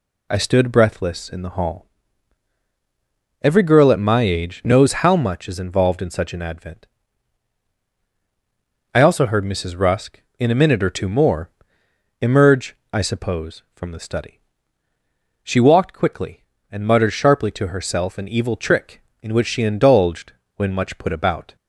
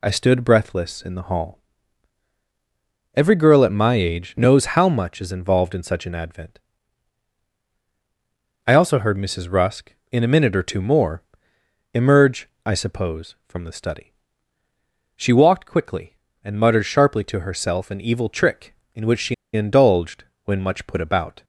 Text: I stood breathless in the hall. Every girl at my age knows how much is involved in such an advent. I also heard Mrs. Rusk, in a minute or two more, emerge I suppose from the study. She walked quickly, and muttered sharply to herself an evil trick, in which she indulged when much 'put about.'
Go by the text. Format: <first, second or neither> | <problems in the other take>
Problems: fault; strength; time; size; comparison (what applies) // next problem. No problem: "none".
first | pauses between "emerge" and "I"; slight; at 12.4 s; 0.16 s long; slight in the first // pauses between "she" and "indulged"; slight; at 19.3 s; 0.19 s long // pauses between "indulged" and "when"; slight; at 20.2 s; 0.20 s long; slight in the first